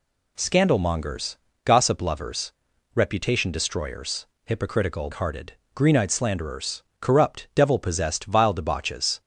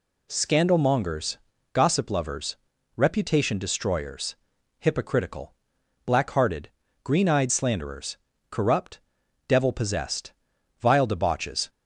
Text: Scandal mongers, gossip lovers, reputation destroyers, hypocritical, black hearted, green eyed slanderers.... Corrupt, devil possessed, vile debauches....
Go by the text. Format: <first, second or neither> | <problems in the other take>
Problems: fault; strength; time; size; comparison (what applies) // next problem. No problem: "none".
second | skips "black"; at 5.1 s